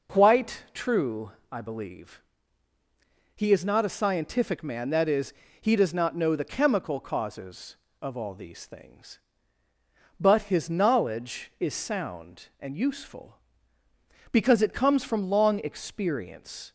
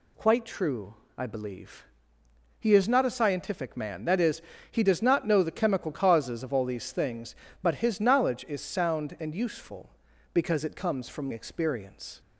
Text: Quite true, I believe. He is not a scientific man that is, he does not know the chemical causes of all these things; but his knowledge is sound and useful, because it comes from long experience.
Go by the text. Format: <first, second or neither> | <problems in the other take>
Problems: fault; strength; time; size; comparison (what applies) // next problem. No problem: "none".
first | skips "long"; at 11.3 s